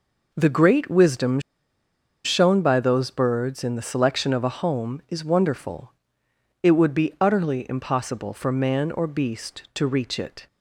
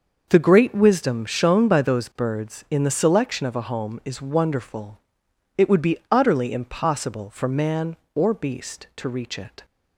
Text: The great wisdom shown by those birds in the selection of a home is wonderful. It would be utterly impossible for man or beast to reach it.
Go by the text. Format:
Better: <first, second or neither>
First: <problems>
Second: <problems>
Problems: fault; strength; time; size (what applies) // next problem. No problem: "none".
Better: second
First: pauses between "wisdom" and "shown"; noticeable; at 1.3 s; 0.84 s long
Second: none